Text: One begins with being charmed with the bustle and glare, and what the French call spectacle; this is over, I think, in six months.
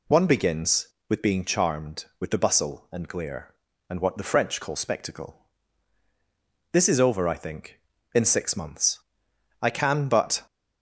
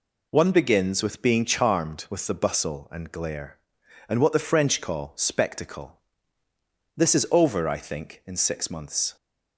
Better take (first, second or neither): second